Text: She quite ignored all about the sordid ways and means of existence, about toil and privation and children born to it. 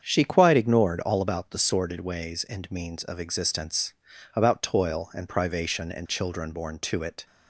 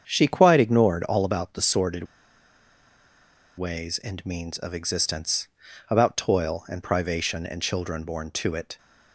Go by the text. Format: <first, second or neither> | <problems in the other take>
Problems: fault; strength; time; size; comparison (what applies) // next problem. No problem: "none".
first | starts louder than the rest; strong; until 1.1 s; 7.5 dB; strong in the first // pauses between "sordid" and "ways"; strong; at 2.0 s; 1.5 s long